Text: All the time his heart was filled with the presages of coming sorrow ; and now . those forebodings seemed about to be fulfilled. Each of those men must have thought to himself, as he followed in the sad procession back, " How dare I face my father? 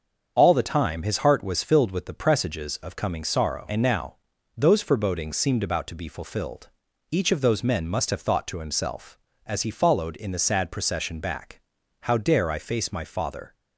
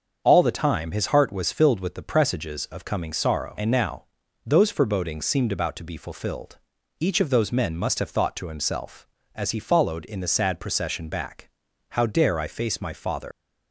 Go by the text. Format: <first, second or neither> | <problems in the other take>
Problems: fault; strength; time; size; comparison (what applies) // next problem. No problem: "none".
first | starts louder than the rest; until 1.2 s; 7 dB; also in the first // leaves "father" unfinished; at 13.3 s; 120 ms